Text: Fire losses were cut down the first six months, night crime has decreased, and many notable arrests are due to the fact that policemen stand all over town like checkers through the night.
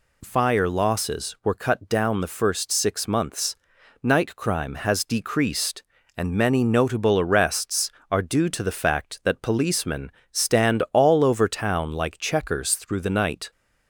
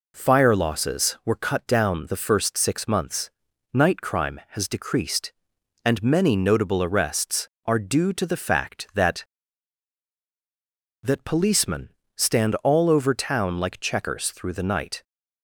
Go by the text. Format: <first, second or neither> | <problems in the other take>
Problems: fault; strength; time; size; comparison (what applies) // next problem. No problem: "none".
first | says "that" twice; at 11.0 s // pauses between "policemen" and "stand"; slight; at 11.8 s; 0.26 s long; slight in the first